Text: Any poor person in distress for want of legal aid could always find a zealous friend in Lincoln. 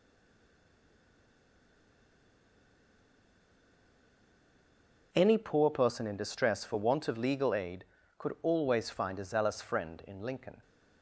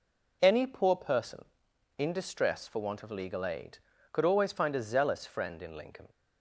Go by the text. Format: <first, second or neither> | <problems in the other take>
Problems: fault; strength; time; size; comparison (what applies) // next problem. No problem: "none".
second | stays silent before the first word; strong; until 5.1 s; 5.1 s long